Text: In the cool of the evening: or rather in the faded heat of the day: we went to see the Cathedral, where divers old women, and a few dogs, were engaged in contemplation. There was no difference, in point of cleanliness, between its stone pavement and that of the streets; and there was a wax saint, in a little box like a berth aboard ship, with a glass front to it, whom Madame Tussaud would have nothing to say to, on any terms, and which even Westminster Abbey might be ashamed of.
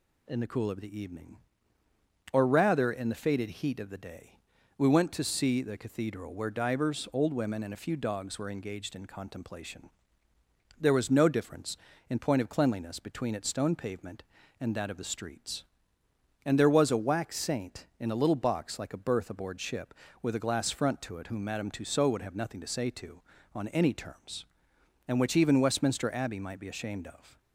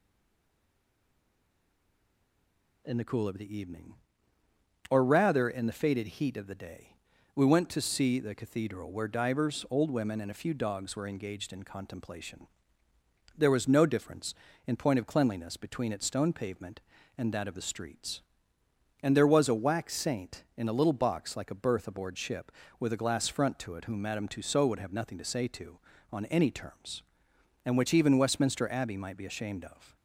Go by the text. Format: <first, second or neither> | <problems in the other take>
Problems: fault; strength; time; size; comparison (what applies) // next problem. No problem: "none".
first | stays silent before the first word; strong; until 2.8 s; 2.8 s long